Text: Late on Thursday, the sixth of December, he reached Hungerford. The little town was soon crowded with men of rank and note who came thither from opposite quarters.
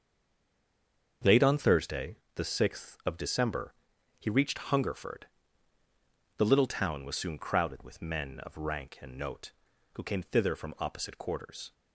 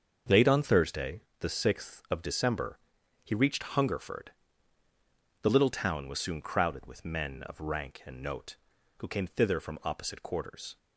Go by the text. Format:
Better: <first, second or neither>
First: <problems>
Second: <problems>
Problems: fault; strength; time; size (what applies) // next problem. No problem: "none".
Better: second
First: stays silent before the first word; noticeable; until 1.2 s; 1.2 s long // starts louder than the rest; until 2.4 s; 6.5 dB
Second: starts louder than the rest; until 1.4 s; 6.5 dB